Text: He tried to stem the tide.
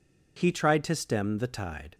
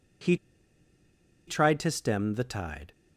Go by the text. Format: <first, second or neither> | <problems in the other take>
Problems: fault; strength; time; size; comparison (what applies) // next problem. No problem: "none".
first | pauses between "He" and "tried"; at 0.3 s; 1.1 s long